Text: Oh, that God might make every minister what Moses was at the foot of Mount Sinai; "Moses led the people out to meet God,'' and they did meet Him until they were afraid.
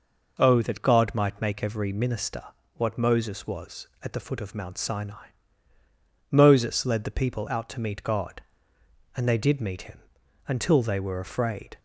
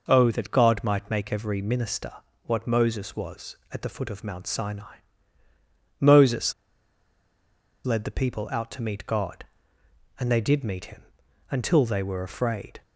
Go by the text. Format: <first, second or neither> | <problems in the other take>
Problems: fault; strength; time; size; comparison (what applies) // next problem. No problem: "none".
first | pauses between "minister" and "what"; slight; at 2.1 s; 0.34 s long; slight in the first // pauses between "Moses" and "led"; strong; at 6.5 s; 1.3 s long // pauses between "Him" and "until"; noticeable; at 11.0 s; 0.48 s long; noticeable in the first